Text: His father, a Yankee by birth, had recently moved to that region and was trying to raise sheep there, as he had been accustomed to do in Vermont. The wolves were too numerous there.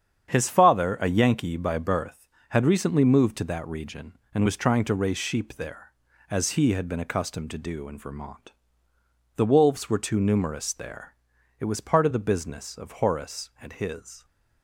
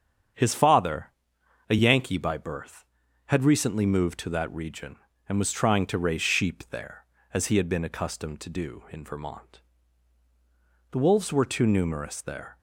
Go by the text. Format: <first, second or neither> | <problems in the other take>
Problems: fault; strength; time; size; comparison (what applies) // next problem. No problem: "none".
second | starts louder than the rest; strong; until 1.3 s; 8.5 dB; strong in the second // goes on to say "It was part of the business of Horace and his"; strong; from 11.5 s on; 2.6 s long